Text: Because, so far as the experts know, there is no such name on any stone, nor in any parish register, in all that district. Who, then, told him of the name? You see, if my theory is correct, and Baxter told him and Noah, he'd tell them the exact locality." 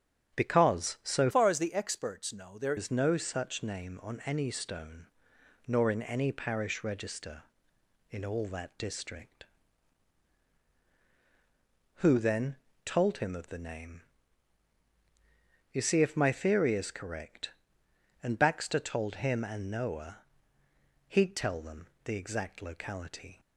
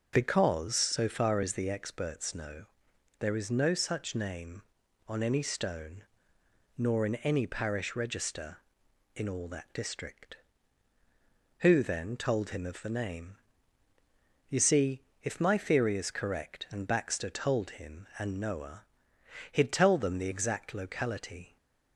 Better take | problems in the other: second | starts louder than the rest; strong; until 1.4 s; 9 dB // changes voice from "far" to "there"; from 1.3 to 2.7 s; 1.4 s long // pauses between "them" and "the"; slight; at 21.8 s; 0.16 s long

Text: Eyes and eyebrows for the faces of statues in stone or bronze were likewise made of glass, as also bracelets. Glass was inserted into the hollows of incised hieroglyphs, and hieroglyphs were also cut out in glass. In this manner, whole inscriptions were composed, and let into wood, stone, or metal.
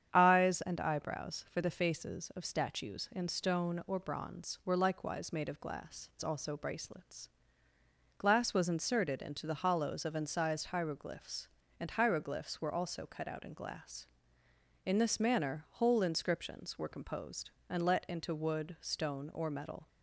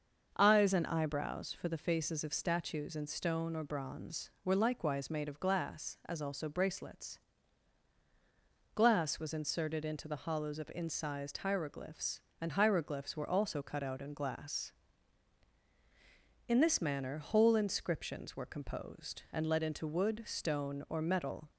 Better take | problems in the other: second | starts louder than the rest; strong; until 1.1 s; 8.5 dB; also in the second // skips "as"; at 6.1 s

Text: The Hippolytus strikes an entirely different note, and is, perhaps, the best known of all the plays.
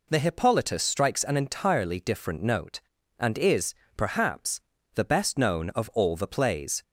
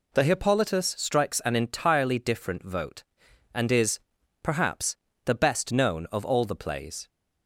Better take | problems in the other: first | says "vote" for "note"; at 2.6 s

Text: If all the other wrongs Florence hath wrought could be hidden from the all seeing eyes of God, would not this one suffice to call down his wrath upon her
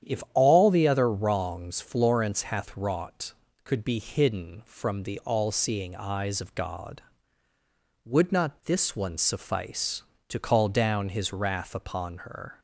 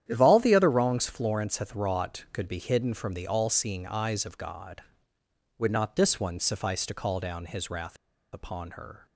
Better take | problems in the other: first | starts louder than the rest; strong; until 1.0 s; 10.5 dB; strong in the first // pauses between "wrath" and "upon"; at 7.9 s; 0.36 s long

